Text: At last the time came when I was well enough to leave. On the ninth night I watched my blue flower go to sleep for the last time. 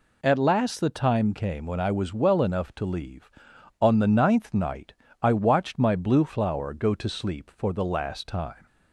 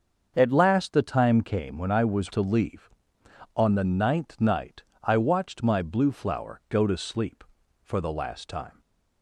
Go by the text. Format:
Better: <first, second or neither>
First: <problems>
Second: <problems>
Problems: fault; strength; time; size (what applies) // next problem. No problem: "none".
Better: first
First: pauses between "night" and "I"; slight; at 4.9 s; 0.28 s long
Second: starts louder than the rest; until 1.3 s; 7 dB // skips "well enough"; at 2.3 s // pauses between "night" and "I"; slight; at 4.8 s; 0.22 s long